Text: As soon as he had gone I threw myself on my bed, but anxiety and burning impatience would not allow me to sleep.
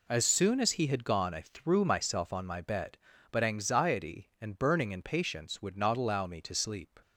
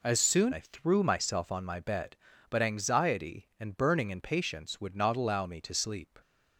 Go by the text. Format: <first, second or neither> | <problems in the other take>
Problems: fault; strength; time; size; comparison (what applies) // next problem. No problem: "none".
first | skips "as he had gone"; at 0.5 s